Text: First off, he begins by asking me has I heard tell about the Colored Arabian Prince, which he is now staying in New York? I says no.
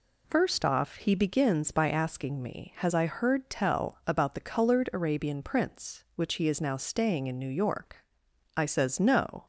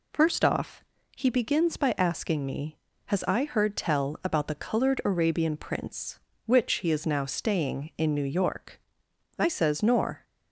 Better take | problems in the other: first | says "nor" for "no"; at 9.8 s

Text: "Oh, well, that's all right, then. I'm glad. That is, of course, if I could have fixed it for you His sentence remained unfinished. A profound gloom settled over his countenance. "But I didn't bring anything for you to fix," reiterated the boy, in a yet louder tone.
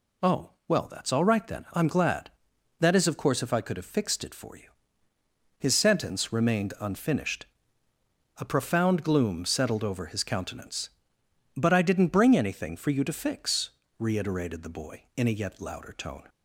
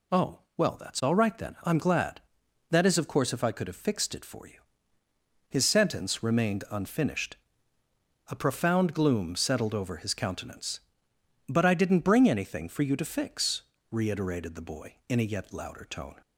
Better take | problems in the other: neither | pauses between "you" and "His"; noticeable; the same in both

